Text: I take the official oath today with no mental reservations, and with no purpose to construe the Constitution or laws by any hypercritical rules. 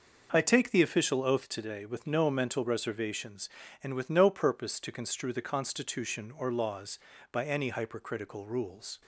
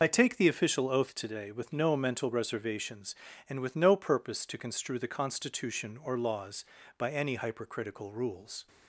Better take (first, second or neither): first